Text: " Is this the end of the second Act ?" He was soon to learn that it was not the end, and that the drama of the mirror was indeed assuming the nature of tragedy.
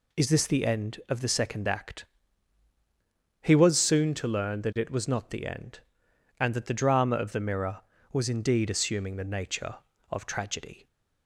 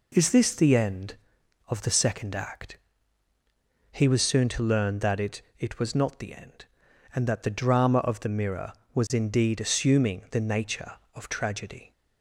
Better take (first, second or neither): first